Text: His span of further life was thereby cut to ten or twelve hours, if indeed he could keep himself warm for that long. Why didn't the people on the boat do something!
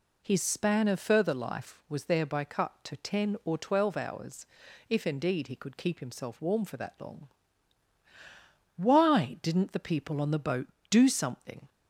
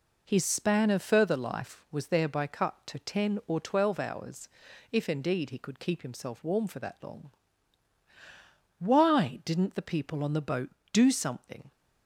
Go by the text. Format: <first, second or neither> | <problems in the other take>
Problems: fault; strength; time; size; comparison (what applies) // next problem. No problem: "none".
first | gets quieter; noticeable; throughout; 5 dB